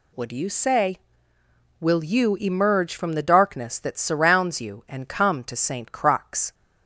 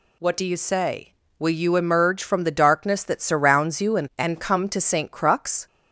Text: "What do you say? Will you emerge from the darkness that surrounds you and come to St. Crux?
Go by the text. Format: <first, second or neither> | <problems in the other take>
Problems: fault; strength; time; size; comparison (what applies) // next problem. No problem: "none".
first | says "and" twice; at 4.1 s